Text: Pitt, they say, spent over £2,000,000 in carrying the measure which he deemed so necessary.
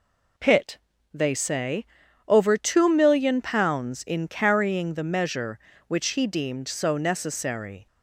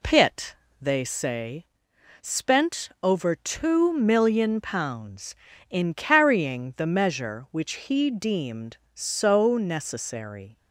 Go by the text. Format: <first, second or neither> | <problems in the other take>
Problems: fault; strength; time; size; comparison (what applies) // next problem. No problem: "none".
second | skips "spent"; at 2.0 s